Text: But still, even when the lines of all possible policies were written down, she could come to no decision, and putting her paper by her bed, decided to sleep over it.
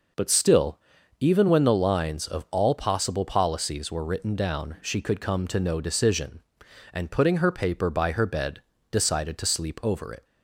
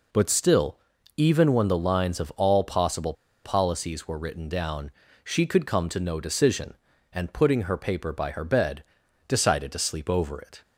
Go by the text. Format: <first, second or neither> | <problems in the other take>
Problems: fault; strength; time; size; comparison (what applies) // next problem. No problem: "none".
first | pauses between "possible" and "policies"; slight; at 3.1 s; 0.31 s long